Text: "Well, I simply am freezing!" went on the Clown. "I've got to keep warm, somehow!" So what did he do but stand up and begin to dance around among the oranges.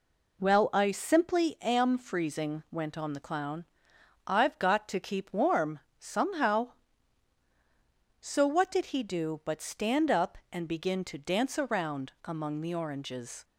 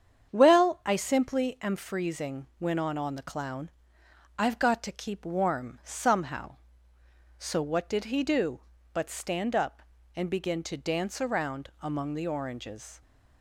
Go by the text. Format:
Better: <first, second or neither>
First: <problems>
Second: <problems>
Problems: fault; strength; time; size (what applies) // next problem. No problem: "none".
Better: first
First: none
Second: starts louder than the rest; strong; until 1.3 s; 8 dB // says "on" twice; at 2.9 s